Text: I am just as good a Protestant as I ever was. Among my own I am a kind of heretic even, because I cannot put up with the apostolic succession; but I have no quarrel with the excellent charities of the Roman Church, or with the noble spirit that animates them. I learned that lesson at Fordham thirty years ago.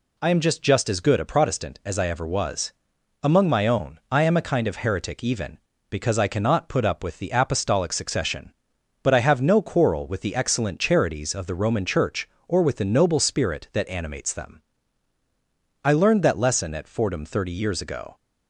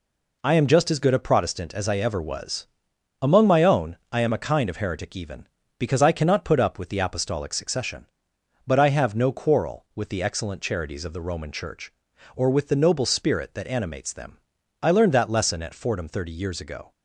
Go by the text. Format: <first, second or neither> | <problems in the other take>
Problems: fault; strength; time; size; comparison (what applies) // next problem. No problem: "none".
second | says "just" twice; at 0.6 s